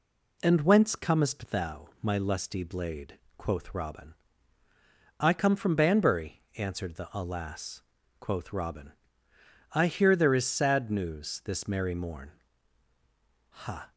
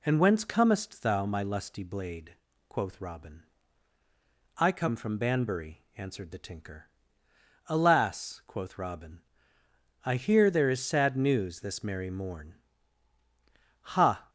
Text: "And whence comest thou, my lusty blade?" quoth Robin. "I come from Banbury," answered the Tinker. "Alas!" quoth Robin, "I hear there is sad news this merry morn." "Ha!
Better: second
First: skips "Tinker"; at 7.1 s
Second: none

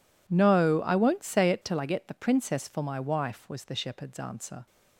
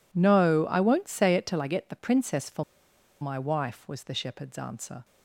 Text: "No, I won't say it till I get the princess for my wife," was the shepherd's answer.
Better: first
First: none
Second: pauses between "for" and "my"; noticeable; at 2.6 s; 0.57 s long

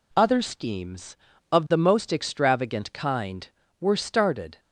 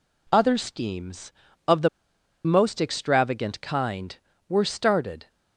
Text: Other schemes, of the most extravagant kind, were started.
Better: first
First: none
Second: pauses between "the" and "most"; noticeable; at 1.8 s; 0.56 s long

